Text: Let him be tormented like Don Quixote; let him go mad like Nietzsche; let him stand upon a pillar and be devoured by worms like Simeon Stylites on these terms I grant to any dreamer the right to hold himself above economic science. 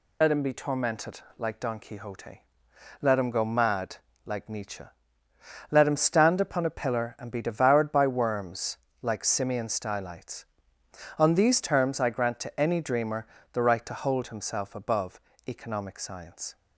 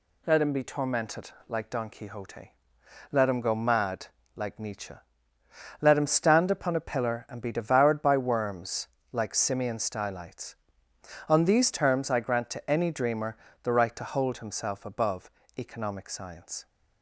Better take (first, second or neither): second